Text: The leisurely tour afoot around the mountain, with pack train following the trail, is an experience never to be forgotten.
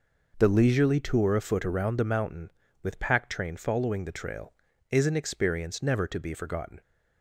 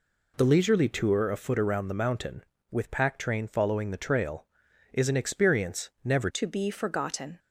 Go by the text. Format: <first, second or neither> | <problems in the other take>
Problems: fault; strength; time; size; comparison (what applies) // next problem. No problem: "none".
first | changes voice at "to"; from 6.2 s on; 1.1 s long